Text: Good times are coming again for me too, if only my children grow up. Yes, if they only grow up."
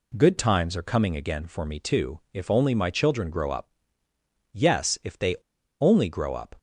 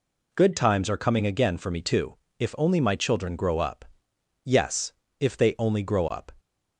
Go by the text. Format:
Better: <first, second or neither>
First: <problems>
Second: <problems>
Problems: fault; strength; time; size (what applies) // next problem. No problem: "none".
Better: second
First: pauses between "they" and "only"; at 5.3 s; 0.45 s long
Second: none